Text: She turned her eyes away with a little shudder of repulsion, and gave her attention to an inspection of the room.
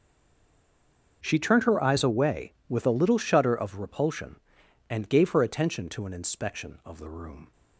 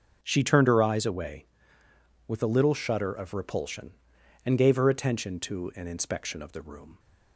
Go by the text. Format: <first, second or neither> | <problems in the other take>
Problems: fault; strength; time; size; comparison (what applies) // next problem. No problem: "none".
second | stays silent before the first word; noticeable; until 1.2 s; 1.2 s long // starts louder than the rest; until 2.2 s; 6.5 dB; noticeable in the second